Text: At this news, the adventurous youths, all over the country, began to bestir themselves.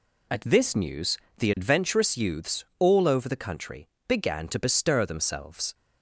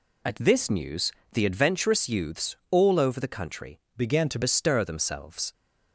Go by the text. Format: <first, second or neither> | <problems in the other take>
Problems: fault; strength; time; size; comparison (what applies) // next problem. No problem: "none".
first | changes voice from "began" to "to"; from 3.9 to 4.3 s; 0.4 s long